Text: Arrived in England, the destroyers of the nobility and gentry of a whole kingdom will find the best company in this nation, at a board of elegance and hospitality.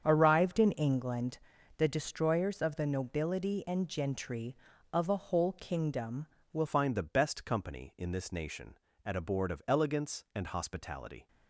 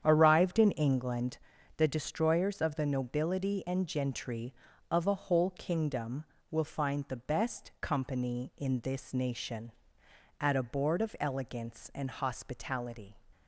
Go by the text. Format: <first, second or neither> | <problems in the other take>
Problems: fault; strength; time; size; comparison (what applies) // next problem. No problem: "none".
second | starts louder than the rest; strong; until 1.0 s; 7.5 dB; strong in the second // changes voice at "find"; from 6.6 s on; 4.6 s long